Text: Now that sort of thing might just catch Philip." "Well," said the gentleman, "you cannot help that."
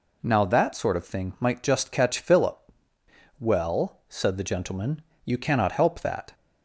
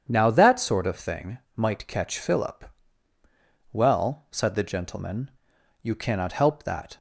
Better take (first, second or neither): first